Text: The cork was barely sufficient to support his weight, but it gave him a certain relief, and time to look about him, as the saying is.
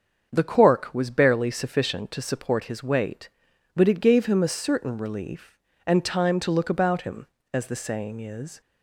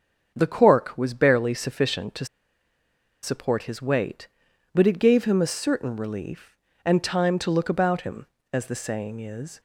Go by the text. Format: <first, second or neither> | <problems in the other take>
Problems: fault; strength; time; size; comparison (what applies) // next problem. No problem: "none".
first | starts louder than the rest; until 1.3 s; 7 dB; also in the first // pauses between "to" and "support"; at 2.2 s; 0.98 s long